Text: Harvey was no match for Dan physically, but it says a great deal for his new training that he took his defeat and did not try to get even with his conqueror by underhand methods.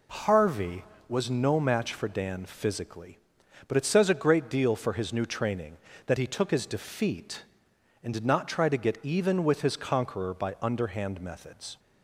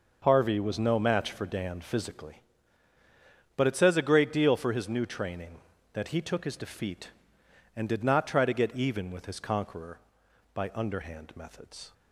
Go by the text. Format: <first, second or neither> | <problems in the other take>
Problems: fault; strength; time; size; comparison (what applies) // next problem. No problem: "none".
neither | none